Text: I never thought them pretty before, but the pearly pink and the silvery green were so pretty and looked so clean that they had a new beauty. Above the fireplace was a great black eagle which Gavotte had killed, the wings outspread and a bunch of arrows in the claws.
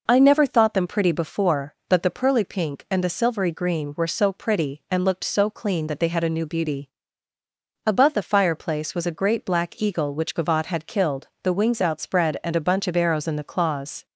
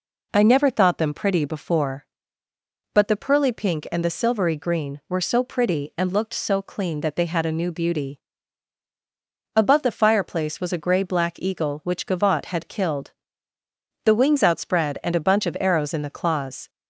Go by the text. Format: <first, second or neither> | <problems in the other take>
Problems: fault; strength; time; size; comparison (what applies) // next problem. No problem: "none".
first | says "grey" for "great"; at 10.8 s